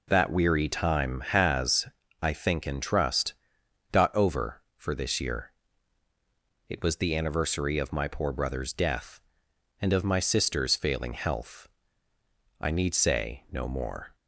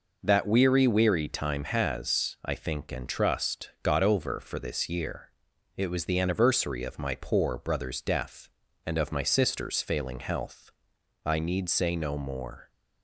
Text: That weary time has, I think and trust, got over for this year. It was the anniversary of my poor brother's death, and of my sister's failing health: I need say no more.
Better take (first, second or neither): first